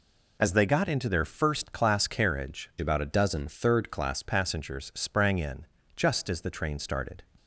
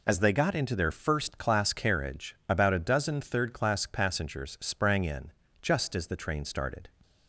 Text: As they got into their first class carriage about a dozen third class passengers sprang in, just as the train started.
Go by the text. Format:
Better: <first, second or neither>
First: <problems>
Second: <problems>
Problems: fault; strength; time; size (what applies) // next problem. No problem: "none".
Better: second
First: changes voice from "about" to "class"; from 2.7 to 4.2 s; 1.5 s long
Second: none